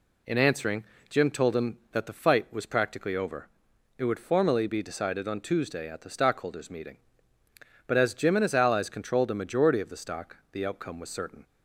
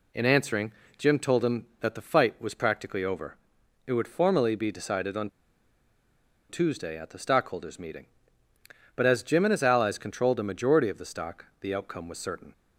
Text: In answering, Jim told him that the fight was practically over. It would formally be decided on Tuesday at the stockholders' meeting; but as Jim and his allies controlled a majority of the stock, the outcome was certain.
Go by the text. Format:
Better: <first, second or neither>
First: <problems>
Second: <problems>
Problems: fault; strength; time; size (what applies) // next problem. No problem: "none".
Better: first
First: none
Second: pauses between "on" and "Tuesday"; at 5.2 s; 1.2 s long